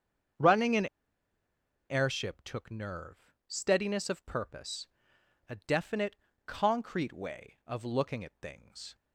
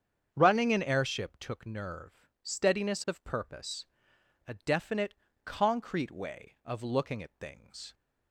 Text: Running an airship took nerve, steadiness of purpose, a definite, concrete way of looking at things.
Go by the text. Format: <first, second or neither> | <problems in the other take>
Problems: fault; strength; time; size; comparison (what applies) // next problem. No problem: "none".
second | starts louder than the rest; strong; until 2.4 s; 7 dB; strong in the second // pauses between "an" and "airship"; at 0.8 s; 1.0 s long